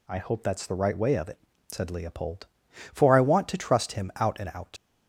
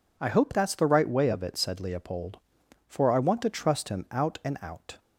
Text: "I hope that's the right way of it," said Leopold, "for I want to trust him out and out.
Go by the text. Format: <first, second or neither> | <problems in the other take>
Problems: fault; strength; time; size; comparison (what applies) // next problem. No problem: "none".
second | leaves "out" unfinished; at 4.7 s; 75 ms